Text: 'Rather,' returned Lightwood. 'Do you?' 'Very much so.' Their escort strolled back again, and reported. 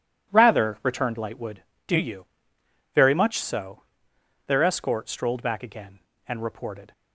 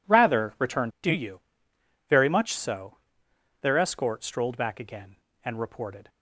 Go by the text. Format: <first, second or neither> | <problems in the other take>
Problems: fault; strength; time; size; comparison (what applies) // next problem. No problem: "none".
first | skips "Lightwood"; at 0.9 s